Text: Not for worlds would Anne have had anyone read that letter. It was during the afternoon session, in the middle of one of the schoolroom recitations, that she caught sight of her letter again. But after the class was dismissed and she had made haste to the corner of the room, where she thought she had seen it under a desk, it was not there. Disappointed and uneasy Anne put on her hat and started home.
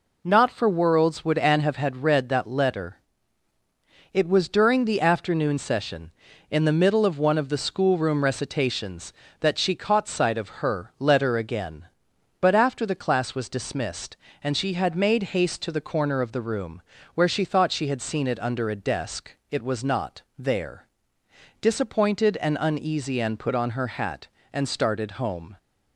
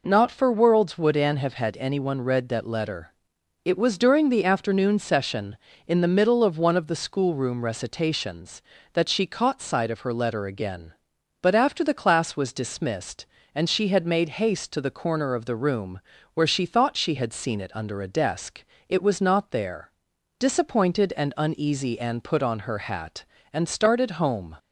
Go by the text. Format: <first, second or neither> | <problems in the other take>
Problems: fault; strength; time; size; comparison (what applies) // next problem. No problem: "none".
second | skips "anyone"; at 2.0 s // pauses between "not" and "there"; slight; at 20.2 s; 0.16 s long